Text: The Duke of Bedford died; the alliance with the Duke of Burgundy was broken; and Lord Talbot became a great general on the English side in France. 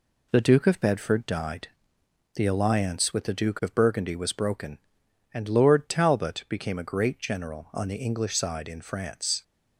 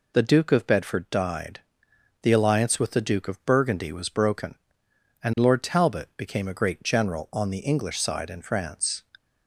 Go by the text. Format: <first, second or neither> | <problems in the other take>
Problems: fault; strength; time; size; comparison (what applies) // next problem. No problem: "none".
second | gets quieter; slight; throughout; 3 dB